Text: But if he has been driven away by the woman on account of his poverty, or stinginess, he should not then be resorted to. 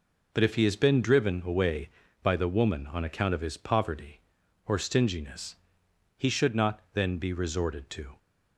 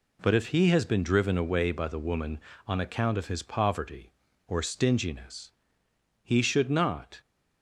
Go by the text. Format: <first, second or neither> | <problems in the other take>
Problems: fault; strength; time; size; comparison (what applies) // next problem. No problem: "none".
first | stops before "then be resorted to"; at 7.2 s